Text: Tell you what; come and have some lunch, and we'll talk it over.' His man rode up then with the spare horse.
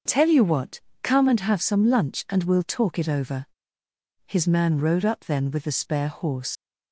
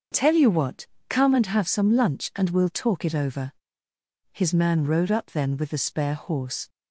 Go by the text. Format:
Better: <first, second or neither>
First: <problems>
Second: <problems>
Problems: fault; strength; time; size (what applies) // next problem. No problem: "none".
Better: second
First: starts louder than the rest; until 1.3 s; 6.5 dB // leaves "horse" unfinished; at 6.5 s; 75 ms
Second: starts louder than the rest; until 1.3 s; 6.5 dB